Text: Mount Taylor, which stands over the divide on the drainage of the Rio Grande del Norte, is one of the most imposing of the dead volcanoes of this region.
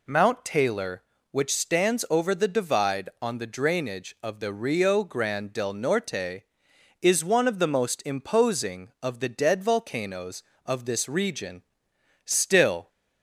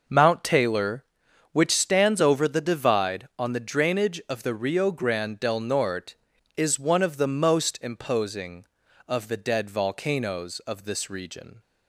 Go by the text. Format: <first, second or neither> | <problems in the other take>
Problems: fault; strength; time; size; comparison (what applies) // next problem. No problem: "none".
second | goes on to say "Still"; noticeable; from 12.2 s on; 0.64 s long